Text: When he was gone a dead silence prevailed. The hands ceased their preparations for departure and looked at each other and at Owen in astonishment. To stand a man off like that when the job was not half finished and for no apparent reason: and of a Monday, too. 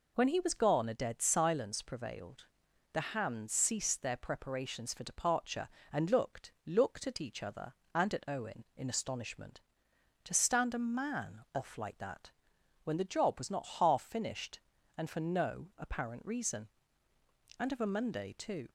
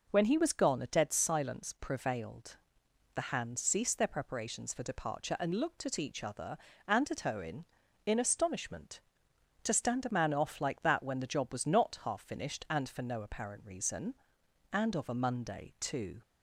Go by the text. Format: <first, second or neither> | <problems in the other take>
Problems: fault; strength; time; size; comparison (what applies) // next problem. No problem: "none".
second | says "looked" twice; at 6.6 s // pauses between "that" and "when"; noticeable; at 12.3 s; 0.54 s long